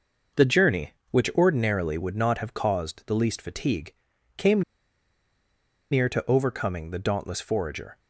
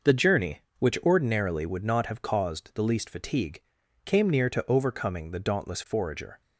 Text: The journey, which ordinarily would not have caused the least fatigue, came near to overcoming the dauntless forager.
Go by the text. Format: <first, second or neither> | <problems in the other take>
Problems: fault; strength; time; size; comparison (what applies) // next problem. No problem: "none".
second | pauses between "came" and "near"; strong; at 4.6 s; 1.2 s long